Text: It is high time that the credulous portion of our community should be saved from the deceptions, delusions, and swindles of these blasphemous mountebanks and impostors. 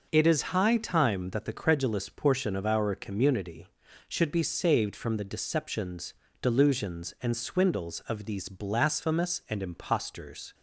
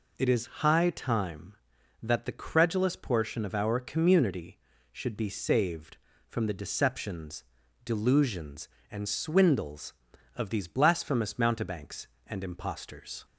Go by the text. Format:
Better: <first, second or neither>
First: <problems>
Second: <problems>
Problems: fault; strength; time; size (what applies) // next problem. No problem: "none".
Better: second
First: skips "mountebanks"; at 9.4 s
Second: none